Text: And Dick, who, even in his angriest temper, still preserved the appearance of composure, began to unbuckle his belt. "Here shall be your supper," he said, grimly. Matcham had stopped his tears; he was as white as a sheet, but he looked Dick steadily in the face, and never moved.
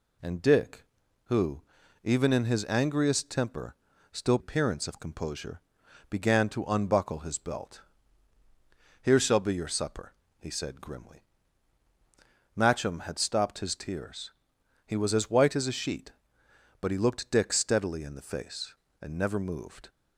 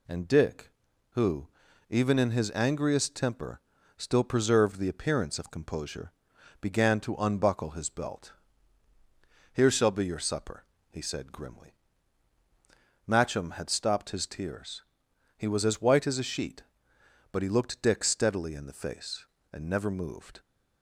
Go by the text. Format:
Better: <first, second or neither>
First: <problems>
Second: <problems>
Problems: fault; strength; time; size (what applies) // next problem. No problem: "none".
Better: second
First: skips "preserved the"; at 4.3 s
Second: none